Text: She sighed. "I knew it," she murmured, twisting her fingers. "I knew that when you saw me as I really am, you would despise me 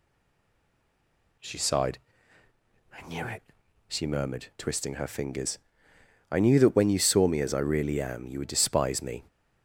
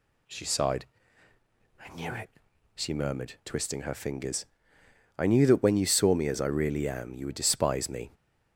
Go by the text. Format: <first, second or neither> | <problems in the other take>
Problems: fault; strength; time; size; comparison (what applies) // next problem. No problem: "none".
second | stays silent before the first word; noticeable; until 1.3 s; 1.3 s long